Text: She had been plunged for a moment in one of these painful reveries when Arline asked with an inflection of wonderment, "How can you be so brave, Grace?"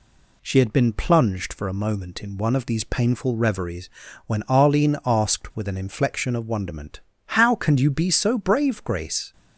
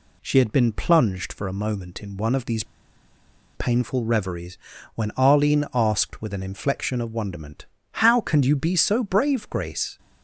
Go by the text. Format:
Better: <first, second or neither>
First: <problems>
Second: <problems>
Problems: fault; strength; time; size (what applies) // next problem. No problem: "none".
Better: first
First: pauses between "reveries" and "when"; slight; at 3.8 s; 0.36 s long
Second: pauses between "these" and "painful"; noticeable; at 2.6 s; 0.91 s long // pauses between "reveries" and "when"; slight; at 4.5 s; 0.36 s long